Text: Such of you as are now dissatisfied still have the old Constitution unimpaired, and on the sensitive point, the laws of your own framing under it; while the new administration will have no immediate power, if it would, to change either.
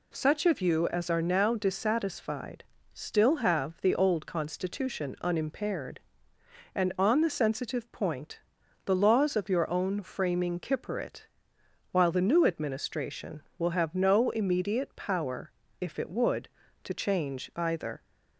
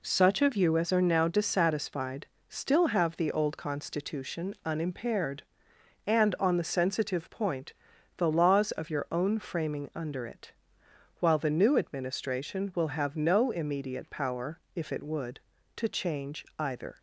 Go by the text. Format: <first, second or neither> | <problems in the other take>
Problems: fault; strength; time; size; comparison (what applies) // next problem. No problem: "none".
second | pauses between "dissatisfied" and "still"; slight; at 2.6 s; 0.28 s long; slight in the second // says "kipper" for "under"; at 10.5 s